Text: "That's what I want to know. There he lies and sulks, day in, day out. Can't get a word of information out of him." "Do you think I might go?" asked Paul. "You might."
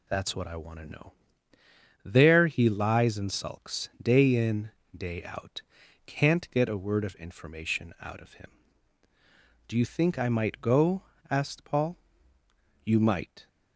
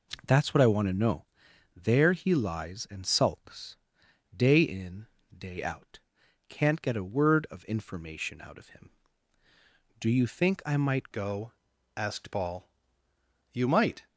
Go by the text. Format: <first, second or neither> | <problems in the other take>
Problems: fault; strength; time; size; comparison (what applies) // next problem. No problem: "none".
first | changes voice at "go"; from 11.1 s on; 2.9 s long